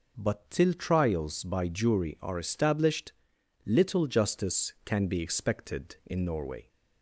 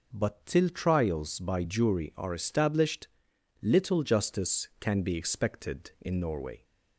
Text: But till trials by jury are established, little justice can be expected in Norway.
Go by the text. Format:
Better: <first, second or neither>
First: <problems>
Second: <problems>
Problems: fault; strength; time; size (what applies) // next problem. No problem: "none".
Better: neither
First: none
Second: none